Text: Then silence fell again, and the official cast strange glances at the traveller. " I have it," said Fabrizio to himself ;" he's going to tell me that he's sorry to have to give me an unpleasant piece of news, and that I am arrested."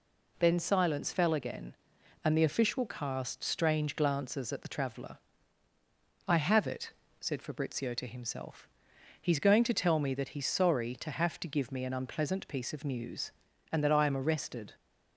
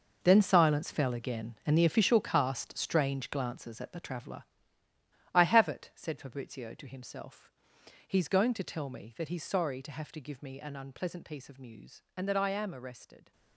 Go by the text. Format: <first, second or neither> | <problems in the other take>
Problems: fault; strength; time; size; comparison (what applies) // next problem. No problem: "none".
first | gets quieter; strong; throughout; 10.5 dB